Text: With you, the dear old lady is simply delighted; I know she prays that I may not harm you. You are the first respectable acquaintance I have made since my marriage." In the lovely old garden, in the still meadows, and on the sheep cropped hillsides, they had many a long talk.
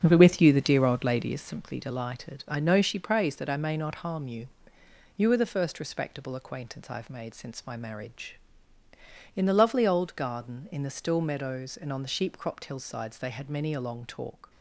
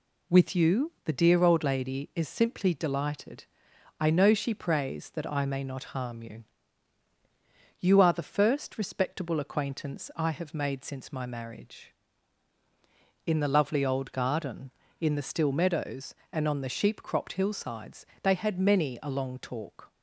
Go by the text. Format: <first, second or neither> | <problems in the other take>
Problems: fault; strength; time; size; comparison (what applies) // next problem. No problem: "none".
second | starts louder than the rest; strong; until 1.5 s; 7.5 dB